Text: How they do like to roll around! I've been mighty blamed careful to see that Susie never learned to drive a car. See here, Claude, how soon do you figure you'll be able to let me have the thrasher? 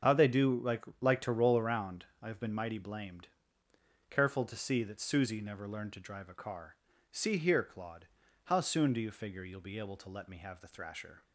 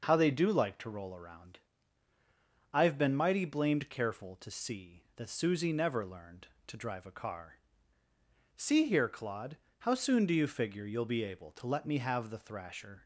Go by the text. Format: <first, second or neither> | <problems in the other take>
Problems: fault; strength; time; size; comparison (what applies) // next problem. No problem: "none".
second | starts louder than the rest; strong; until 1.2 s; 7.5 dB // says "like" twice; at 0.9 s // pauses between "blamed" and "careful"; noticeable; at 3.2 s; 0.82 s long